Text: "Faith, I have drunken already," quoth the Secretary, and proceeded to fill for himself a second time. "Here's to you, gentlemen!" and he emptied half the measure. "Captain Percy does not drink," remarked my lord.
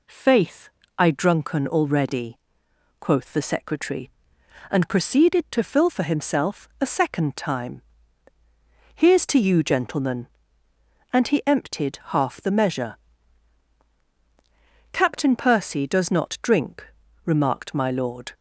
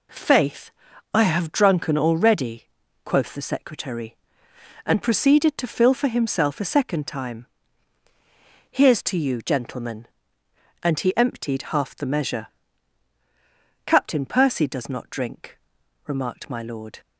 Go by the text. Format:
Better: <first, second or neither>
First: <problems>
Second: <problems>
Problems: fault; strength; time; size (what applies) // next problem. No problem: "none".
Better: second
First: skips "have"; at 1.0 s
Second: none